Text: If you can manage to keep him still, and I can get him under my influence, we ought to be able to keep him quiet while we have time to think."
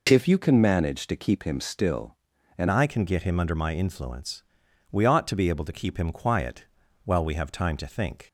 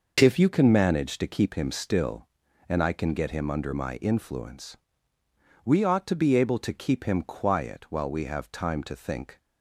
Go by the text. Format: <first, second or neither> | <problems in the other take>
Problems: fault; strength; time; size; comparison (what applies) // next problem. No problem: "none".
second | changes voice at "I"; from 2.6 s on; 5.6 s long // pauses between "quiet" and "while"; at 6.6 s; 0.40 s long